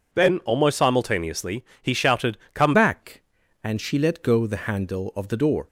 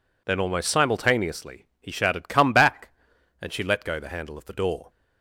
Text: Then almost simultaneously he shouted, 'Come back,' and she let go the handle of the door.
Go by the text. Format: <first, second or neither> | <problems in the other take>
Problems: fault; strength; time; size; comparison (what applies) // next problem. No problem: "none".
second | pauses between "simultaneously" and "he"; slight; at 1.6 s; 0.18 s long; slight in the second // changes voice at "back"; from 2.7 s on; 2.9 s long